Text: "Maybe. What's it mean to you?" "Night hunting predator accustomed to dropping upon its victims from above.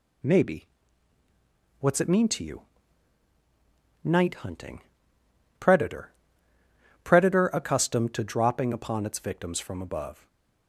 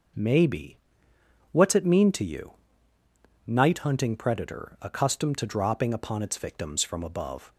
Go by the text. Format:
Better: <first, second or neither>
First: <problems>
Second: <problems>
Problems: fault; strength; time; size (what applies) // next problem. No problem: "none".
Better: second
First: pauses between "hunting" and "predator"; noticeable; at 4.8 s; 0.76 s long // says "predator" twice; at 7.0 s // stays silent after the last word; slight; from 10.1 s on; 0.5 s long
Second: none